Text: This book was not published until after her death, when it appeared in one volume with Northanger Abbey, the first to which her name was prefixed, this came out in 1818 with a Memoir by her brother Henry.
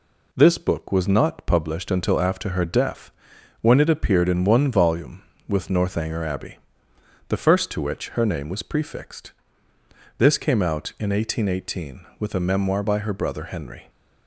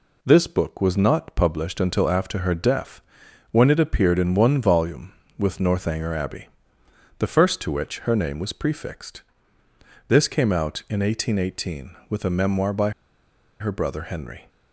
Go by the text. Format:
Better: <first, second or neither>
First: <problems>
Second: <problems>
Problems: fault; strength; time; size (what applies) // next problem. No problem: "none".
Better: first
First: none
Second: pauses between "by" and "her"; noticeable; at 12.9 s; 0.69 s long